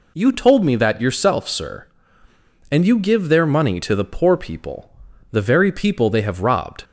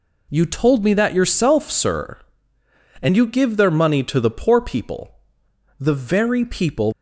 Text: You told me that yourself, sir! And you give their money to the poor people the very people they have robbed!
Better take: first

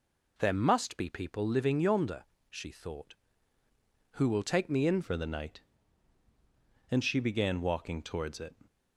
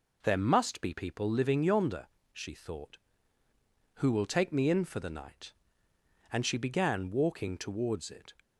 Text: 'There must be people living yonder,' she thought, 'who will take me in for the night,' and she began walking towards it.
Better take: second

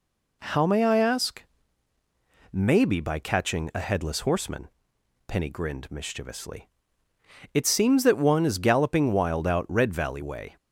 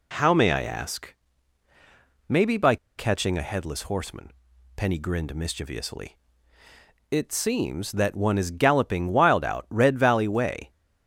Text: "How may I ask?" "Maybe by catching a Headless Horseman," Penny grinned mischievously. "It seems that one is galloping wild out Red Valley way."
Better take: first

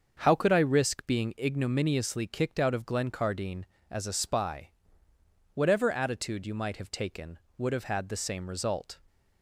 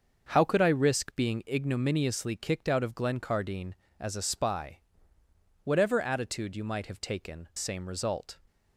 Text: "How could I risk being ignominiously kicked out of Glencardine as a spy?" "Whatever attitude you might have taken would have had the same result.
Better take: first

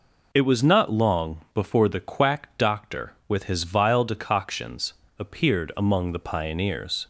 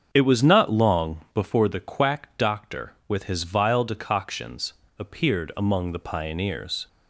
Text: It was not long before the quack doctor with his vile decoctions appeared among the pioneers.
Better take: first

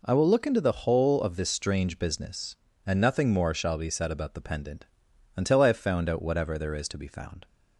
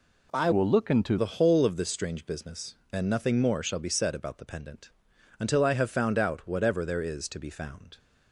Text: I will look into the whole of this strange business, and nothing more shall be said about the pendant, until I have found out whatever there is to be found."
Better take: first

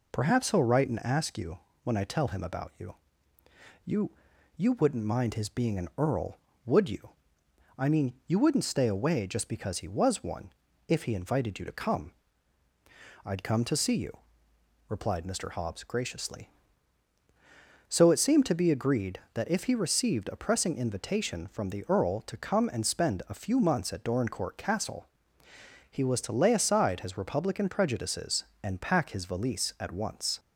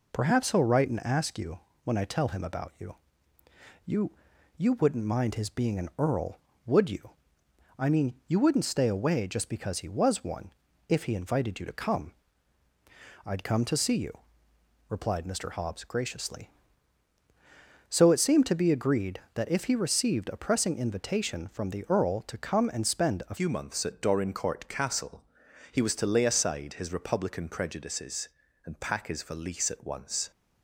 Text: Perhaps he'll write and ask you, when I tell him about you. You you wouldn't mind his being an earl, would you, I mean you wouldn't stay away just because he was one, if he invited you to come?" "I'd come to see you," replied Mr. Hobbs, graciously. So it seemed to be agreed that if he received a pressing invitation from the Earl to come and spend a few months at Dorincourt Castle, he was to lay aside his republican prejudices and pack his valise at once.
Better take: first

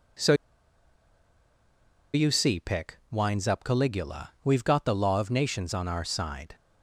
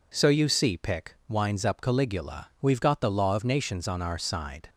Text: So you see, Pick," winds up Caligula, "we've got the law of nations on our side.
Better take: second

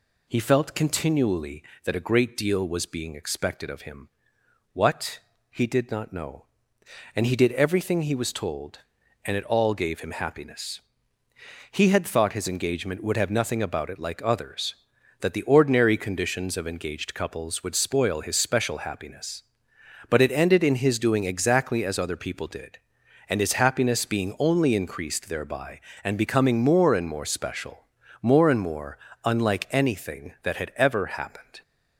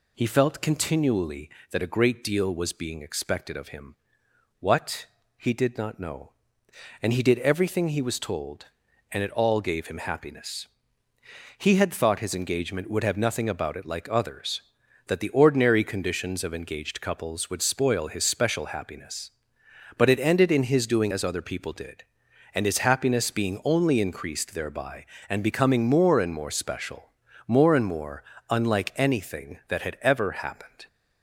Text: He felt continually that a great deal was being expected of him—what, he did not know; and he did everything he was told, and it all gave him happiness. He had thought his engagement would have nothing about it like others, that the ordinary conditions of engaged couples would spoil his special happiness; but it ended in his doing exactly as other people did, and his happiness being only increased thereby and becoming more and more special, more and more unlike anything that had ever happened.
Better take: first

